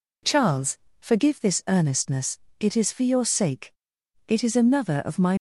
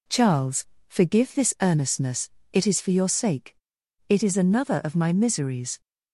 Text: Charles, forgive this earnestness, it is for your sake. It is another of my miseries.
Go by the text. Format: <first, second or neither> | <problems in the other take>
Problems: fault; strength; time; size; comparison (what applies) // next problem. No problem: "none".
second | stops before "miseries"; at 5.3 s